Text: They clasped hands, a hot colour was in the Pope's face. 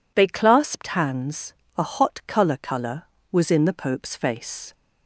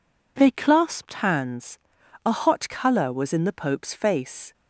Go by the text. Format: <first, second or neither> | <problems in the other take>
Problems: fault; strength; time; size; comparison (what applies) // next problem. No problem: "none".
second | says "colour" twice; at 2.5 s